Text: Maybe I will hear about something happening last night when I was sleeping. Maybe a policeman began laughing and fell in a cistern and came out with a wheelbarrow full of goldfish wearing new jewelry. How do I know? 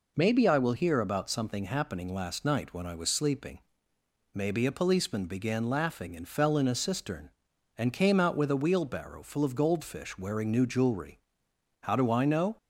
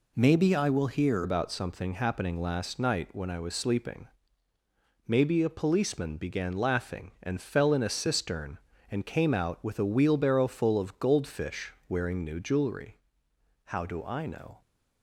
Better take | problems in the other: first | changes voice at "about"; from 1.2 s on; 13.4 s long // pauses between "goldfish" and "wearing"; slight; at 11.7 s; 0.16 s long

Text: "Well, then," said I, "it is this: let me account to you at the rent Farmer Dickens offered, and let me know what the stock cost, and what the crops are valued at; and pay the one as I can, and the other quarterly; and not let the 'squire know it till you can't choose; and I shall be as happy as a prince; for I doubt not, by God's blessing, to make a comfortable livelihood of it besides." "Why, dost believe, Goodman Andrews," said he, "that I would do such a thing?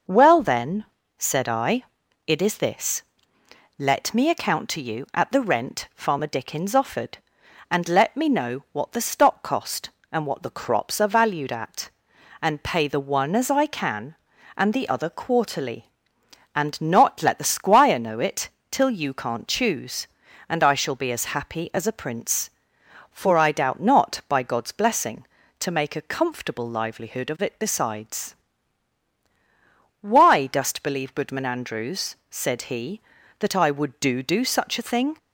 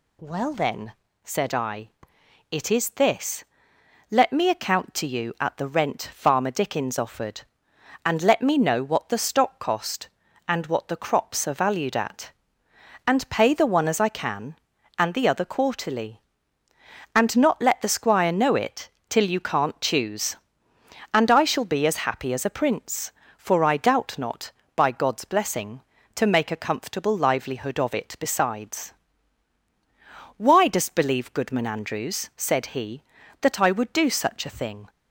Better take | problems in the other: second | starts louder than the rest; noticeable; until 1.4 s; 6 dB // pauses between "it" and "till"; slight; at 18.4 s; 0.22 s long; slight in the second // says "do" twice; at 34.2 s

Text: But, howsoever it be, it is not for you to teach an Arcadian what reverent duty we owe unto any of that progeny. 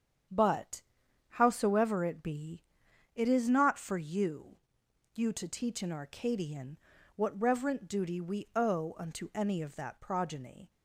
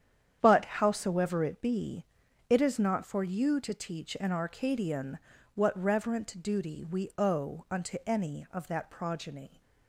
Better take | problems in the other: second | starts louder than the rest; strong; until 1.7 s; 8 dB; strong in the second // says "you" twice; at 5.1 s // pauses between "Arcadian" and "what"; at 6.7 s; 0.38 s long; slight in the second

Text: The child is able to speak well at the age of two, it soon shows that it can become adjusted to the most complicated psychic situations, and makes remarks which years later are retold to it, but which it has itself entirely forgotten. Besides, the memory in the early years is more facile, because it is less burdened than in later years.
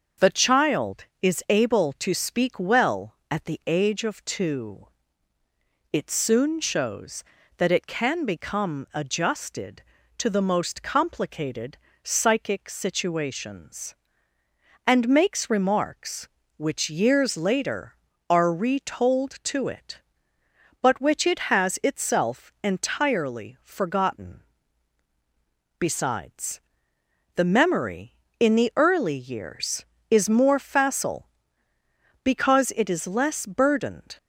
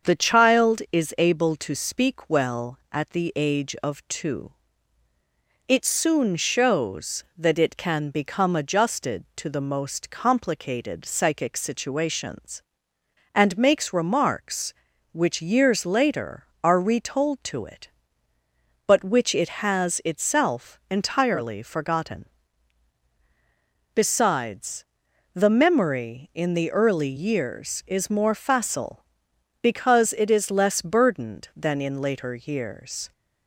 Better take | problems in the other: second | starts louder than the rest; until 1.3 s; 6 dB; also in the second // pauses between "complicated" and "psychic"; slight; at 11.7 s; 0.24 s long // stops before "than in later years"; at 34.1 s

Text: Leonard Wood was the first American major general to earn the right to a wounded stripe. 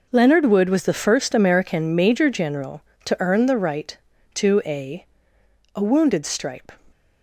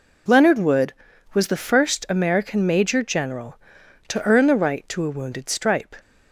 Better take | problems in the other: second | says "a" twice; at 5.7 s

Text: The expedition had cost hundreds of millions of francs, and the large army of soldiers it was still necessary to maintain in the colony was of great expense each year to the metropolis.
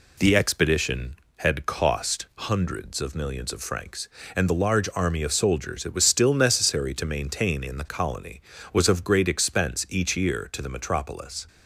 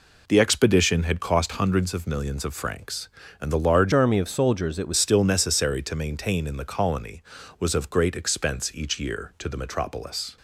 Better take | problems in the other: first | changes voice from "army" to "was"; from 3.9 to 4.9 s; 1.0 s long

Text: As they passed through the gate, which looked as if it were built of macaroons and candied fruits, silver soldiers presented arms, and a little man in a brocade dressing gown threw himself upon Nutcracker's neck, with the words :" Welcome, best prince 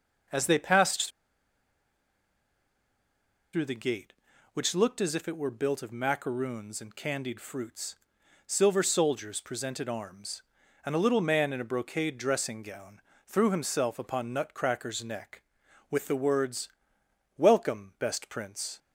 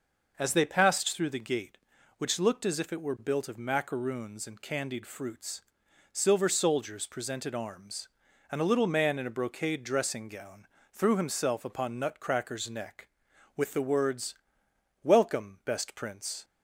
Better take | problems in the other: second | pauses between "passed" and "through"; strong; at 1.0 s; 2.4 s long // pauses between "gown" and "threw"; slight; at 13.0 s; 0.26 s long; slight in the second

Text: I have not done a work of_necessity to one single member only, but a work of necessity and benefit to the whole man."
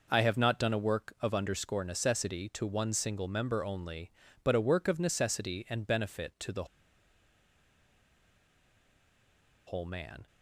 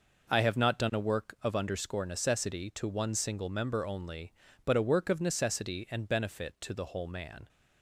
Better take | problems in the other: second | pauses between "the" and "whole"; strong; at 6.6 s; 3.0 s long

